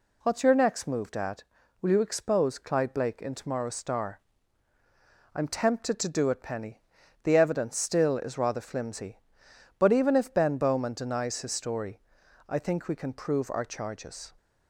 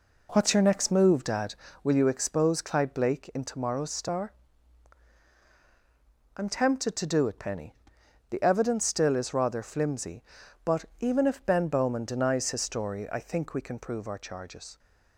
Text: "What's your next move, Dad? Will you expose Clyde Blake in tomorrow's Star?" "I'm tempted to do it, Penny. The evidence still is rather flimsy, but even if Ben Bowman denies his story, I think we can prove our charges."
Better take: first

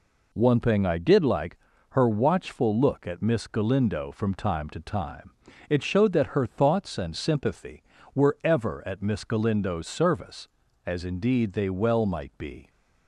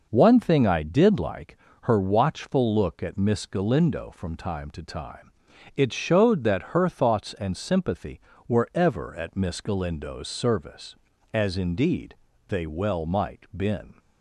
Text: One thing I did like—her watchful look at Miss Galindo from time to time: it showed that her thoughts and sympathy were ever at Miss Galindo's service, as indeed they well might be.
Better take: first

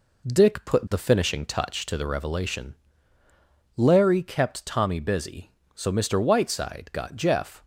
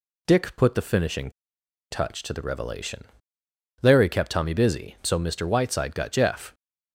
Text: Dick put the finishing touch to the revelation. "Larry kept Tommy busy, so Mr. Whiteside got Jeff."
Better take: first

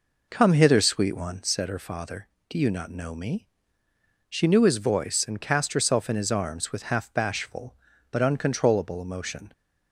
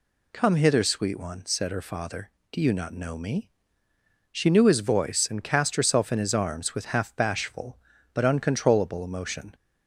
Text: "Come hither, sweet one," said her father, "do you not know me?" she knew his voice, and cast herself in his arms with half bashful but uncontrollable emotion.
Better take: second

